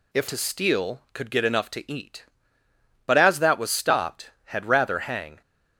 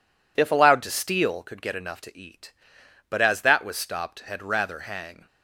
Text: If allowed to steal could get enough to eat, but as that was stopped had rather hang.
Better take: second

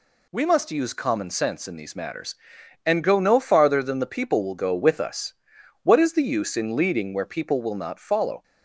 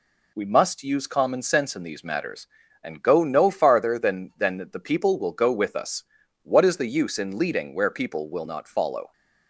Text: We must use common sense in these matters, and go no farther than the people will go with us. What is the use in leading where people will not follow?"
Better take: first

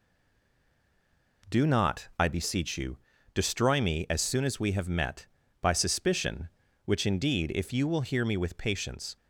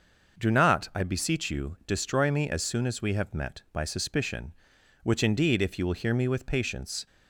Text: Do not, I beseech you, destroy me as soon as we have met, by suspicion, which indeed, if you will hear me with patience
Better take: second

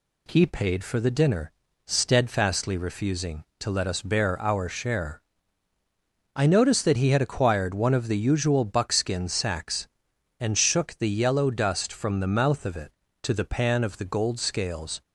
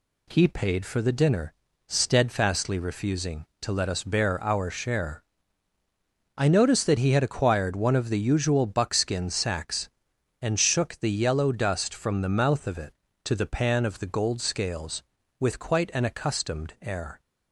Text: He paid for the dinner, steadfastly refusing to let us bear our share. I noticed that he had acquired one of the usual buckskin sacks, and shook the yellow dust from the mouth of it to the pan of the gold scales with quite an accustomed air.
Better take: second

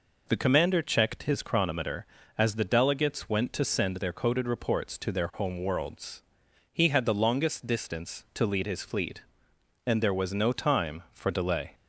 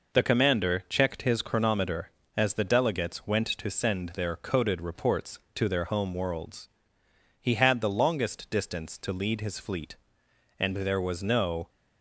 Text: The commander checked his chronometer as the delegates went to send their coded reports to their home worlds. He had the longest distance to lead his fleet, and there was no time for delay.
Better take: first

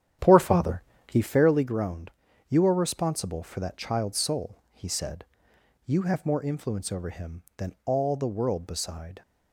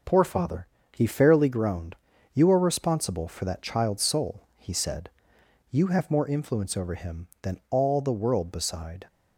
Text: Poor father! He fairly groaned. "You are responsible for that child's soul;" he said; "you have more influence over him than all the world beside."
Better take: second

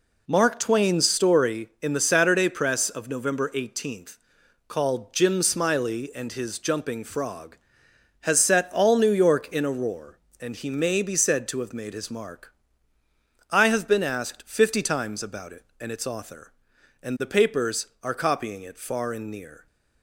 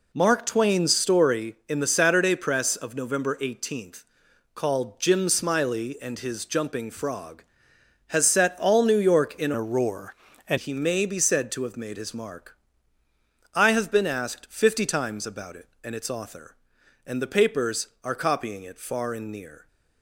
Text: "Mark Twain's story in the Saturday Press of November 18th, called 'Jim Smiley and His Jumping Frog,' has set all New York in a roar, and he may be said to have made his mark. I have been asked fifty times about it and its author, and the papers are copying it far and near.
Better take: first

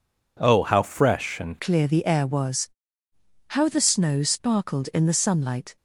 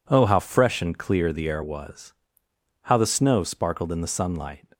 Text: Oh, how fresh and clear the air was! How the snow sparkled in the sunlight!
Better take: second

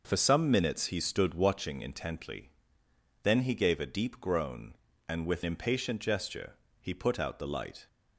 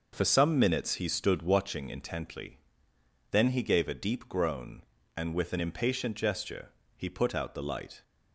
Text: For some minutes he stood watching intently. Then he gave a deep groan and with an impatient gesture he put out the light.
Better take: second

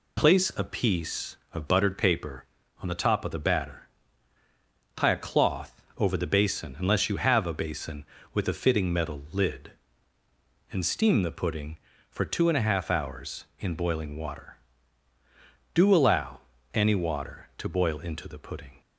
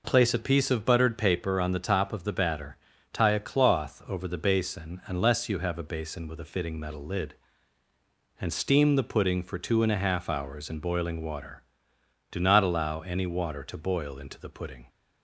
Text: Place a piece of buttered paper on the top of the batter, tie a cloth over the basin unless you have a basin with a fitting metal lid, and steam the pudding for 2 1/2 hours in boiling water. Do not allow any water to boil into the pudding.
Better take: second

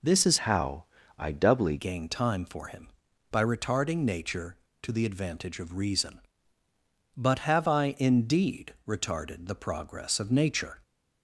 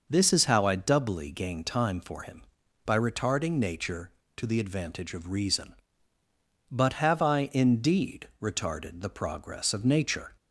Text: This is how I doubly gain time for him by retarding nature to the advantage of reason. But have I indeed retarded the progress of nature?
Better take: second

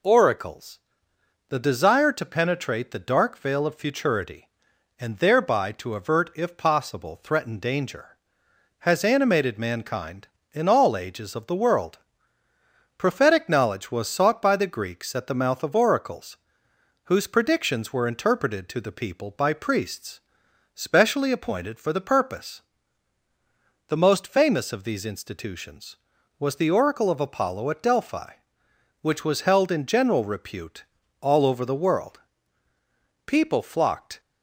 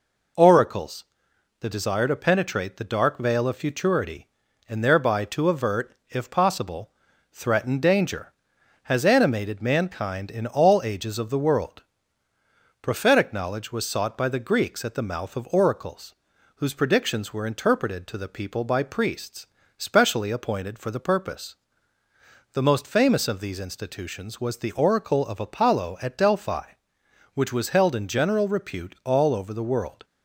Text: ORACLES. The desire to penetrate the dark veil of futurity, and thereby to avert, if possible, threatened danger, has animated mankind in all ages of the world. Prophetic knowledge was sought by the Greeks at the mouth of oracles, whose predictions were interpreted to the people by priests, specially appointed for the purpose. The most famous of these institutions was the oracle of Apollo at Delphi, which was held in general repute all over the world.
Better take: second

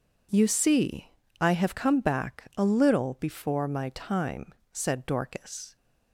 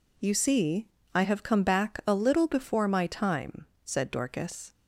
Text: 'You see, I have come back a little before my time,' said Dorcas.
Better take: neither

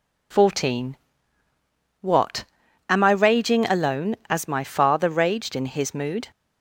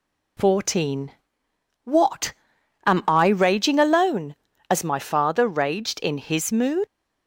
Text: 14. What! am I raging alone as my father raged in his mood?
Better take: first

